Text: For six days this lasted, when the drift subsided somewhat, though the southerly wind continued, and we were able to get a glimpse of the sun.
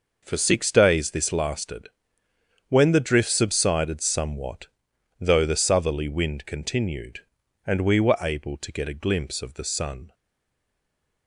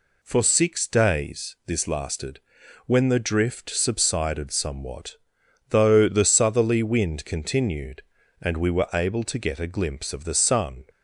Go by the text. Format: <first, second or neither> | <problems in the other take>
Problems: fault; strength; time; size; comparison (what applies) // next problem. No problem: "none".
second | stays silent after the last word; noticeable; from 10.1 s on; 1.1 s long